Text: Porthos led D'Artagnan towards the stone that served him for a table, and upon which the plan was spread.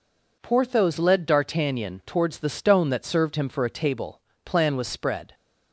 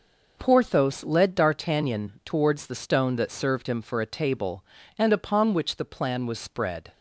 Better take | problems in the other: second | skips "and upon which the"; at 4.3 s

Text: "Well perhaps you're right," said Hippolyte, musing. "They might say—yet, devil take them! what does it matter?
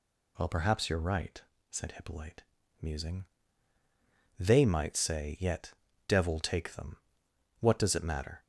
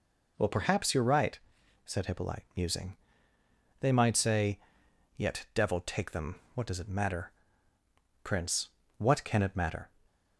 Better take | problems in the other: first | goes on to say "prince what can it matter"; from 8.2 s on; 1.6 s long // stays silent after the last word; slight; from 9.8 s on; 0.5 s long

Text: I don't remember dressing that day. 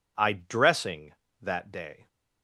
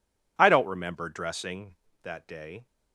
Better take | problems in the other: second | skips "don't remember"; at 0.3 s

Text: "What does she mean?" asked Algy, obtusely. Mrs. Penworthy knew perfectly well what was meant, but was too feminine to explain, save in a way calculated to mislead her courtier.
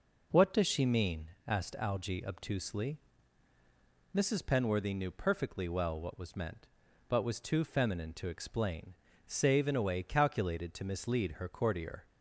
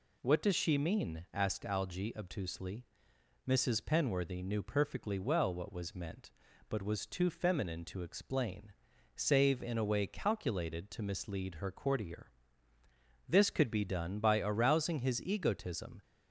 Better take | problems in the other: first | goes on to say "This could be done by arousing his egotism"; strong; from 13.2 s on; 2.7 s long

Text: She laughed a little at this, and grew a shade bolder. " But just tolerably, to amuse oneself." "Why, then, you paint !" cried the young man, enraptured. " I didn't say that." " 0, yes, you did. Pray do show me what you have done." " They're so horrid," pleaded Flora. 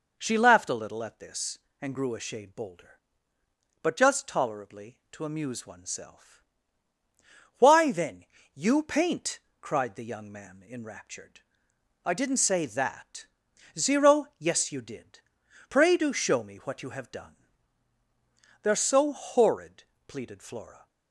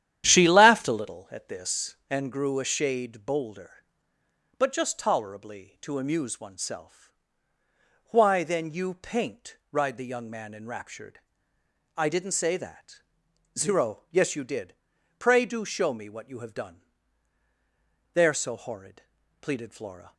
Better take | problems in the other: first | starts louder than the rest; strong; until 1.2 s; 11 dB

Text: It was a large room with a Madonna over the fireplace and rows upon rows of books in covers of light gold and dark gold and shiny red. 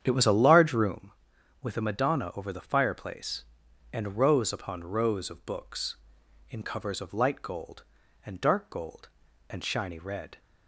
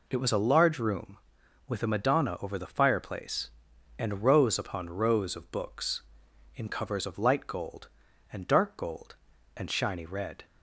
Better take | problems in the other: second | starts louder than the rest; strong; until 0.9 s; 8.5 dB

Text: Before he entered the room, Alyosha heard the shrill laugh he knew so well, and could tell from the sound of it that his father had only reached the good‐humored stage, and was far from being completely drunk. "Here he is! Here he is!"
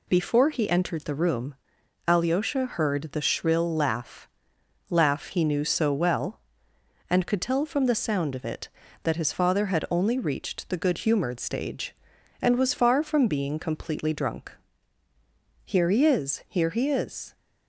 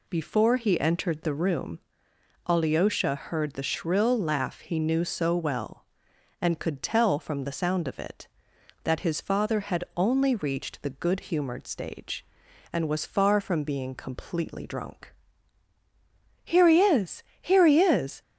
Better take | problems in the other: second | says "laugh" twice; at 4.9 s

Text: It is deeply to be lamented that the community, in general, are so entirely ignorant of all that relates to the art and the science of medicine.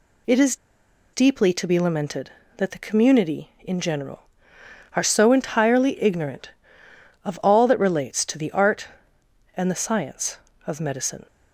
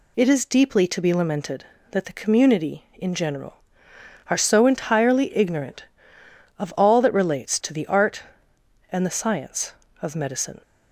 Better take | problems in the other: second | pauses between "is" and "deeply"; noticeable; at 0.5 s; 0.58 s long

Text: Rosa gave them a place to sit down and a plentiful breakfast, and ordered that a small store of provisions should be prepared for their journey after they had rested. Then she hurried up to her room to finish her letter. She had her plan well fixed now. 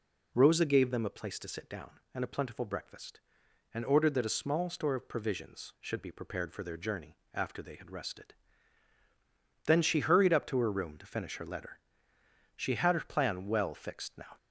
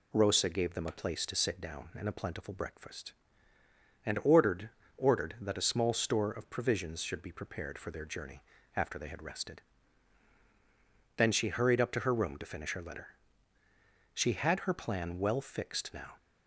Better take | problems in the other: first | says "ordered" twice; at 4.9 s // pauses between "journey" and "after"; slight; at 8.4 s; 0.34 s long; slight in the first

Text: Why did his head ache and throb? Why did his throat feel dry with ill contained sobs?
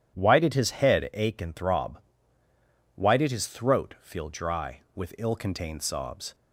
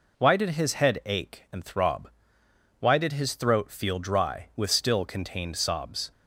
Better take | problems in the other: first | says "still" for "ill"; at 4.7 s

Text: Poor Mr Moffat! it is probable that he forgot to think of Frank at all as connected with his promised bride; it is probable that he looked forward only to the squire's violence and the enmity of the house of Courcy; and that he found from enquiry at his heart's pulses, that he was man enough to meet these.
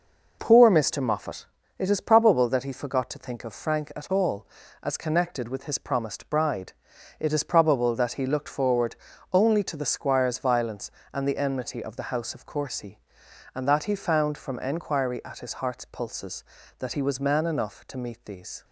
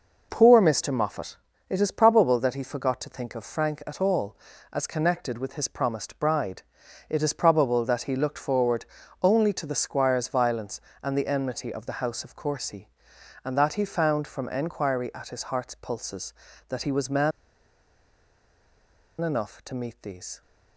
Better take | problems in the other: first | pauses between "forward" and "only"; at 8.8 s; 0.38 s long; also in the first // pauses between "man" and "enough"; strong; at 17.3 s; 1.9 s long

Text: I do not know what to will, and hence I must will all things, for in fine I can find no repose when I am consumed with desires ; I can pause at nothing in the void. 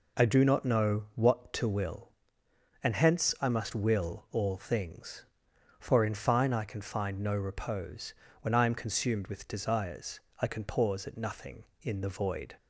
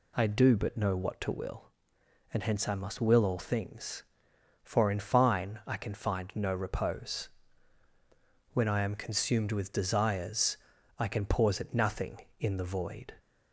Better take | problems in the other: first | says "but" for "not"; at 0.5 s // pauses between "repose" and "when"; at 7.2 s; 1.2 s long; slight in the first

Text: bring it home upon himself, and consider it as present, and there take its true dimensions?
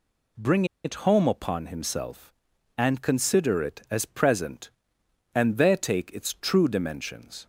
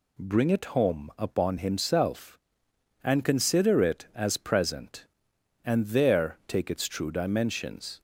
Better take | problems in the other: second | pauses between "bring" and "it"; slight; at 0.6 s; 0.19 s long

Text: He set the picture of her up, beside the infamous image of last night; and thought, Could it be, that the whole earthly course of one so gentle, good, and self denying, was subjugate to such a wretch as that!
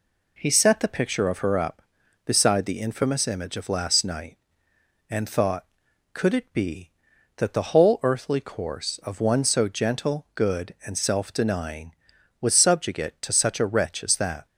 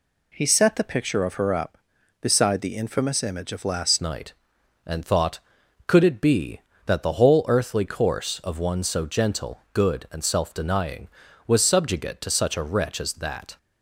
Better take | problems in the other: first | changes voice at "night"; from 3.9 s on; 9.6 s long

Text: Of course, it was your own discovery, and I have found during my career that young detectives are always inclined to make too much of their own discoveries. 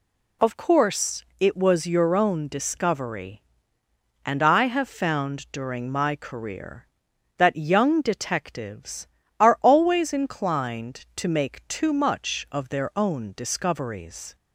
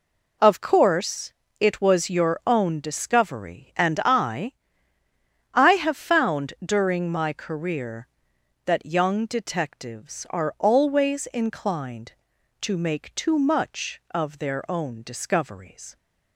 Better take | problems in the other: first | says "I" twice; at 5.5 s

